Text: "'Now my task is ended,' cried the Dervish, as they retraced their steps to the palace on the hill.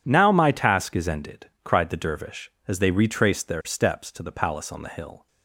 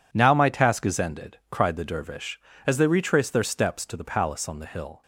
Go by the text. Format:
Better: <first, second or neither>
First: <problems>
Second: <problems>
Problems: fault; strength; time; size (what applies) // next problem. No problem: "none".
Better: neither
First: none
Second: none